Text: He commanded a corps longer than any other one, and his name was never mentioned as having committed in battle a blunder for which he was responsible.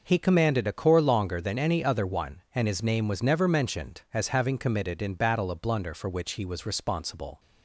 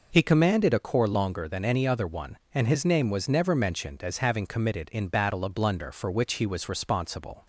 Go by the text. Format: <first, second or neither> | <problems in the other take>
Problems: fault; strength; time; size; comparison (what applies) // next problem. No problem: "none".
neither | none